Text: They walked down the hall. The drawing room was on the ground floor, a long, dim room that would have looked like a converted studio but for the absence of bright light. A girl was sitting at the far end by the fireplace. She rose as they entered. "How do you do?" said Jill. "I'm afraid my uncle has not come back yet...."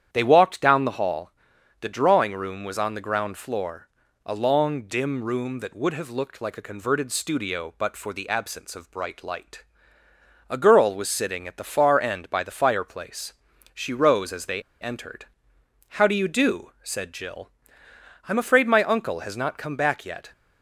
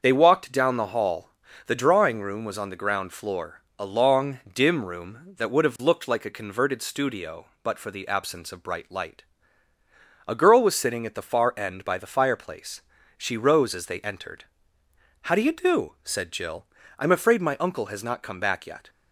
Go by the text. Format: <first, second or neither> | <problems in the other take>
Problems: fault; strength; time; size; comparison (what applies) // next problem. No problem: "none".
second | starts louder than the rest; strong; until 1.1 s; 10 dB; also in the second // pauses between "they" and "entered"; slight; at 14.6 s; 0.19 s long